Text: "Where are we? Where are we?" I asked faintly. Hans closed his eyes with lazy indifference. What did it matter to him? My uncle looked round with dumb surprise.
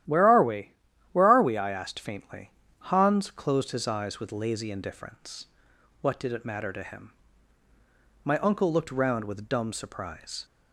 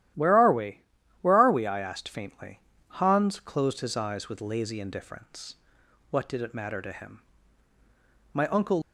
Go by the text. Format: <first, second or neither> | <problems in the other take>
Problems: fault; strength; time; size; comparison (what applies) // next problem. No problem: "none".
first | starts louder than the rest; strong; until 1.5 s; 12.5 dB; strong in the first // stops before "looked round with dumb surprise"; at 8.8 s